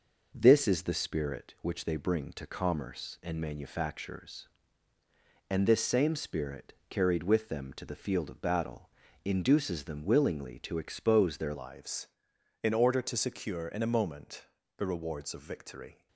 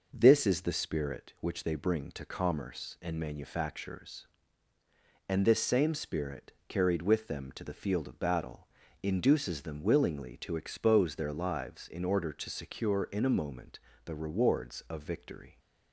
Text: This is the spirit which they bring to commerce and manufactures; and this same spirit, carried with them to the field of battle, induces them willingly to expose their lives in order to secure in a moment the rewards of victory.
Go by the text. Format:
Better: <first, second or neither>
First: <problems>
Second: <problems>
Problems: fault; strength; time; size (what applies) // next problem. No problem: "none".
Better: second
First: changes voice at "lives"; from 11.5 s on; 4.5 s long // pauses between "moment" and "the"; slight; at 14.4 s; 0.30 s long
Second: pauses between "moment" and "the"; slight; at 13.7 s; 0.28 s long